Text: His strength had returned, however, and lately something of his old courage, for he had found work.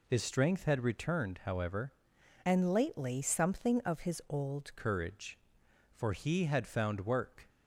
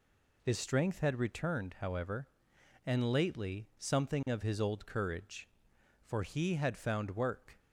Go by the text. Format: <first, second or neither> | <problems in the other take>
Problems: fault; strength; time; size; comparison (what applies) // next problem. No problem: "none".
second | changes voice from "and" to "old"; from 2.4 to 4.7 s; 2.3 s long